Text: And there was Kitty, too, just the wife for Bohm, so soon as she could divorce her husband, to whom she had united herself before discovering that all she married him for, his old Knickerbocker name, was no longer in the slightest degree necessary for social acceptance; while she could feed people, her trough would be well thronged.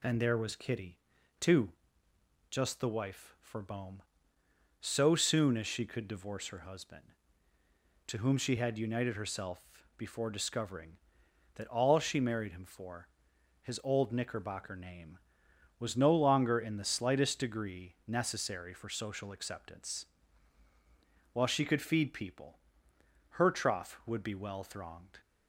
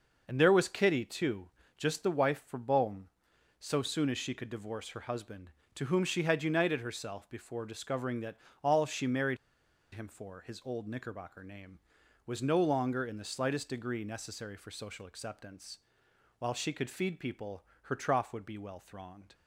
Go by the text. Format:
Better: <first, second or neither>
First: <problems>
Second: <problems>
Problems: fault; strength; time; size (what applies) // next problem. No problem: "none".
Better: first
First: none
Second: pauses between "that" and "all"; slight; at 8.3 s; 0.26 s long // pauses between "married" and "him"; noticeable; at 9.3 s; 0.56 s long